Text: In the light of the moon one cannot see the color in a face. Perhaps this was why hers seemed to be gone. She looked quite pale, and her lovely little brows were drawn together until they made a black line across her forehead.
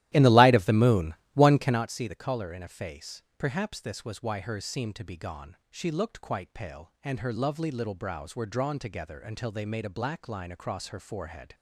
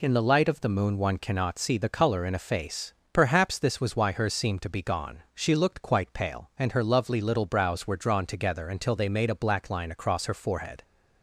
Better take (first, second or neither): second